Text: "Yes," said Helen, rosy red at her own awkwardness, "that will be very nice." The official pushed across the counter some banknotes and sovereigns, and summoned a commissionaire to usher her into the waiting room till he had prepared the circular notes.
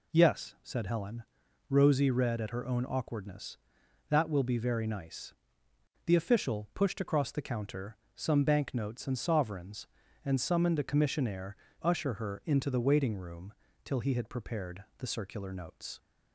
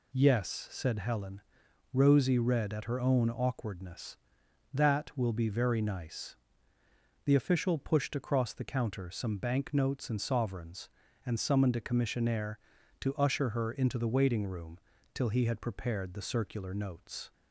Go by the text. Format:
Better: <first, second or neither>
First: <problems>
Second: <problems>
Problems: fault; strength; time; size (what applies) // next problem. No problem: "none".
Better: second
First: pauses between "counter" and "some"; slight; at 7.9 s; 0.18 s long // skips "to"; at 11.6 s // pauses between "room" and "till"; slight; at 13.5 s; 0.32 s long // pauses between "prepared" and "the"; slight; at 14.8 s; 0.16 s long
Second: pauses between "room" and "till"; slight; at 14.7 s; 0.34 s long